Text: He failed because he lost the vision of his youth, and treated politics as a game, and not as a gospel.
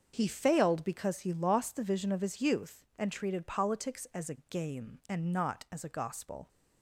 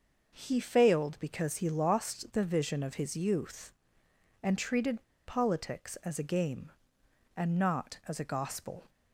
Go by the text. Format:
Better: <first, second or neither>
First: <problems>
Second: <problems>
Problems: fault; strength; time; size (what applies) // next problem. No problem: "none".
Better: first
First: starts louder than the rest; until 1.1 s; 6.5 dB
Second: starts louder than the rest; until 1.4 s; 6 dB // pauses between "treated" and "politics"; slight; at 5.0 s; 0.23 s long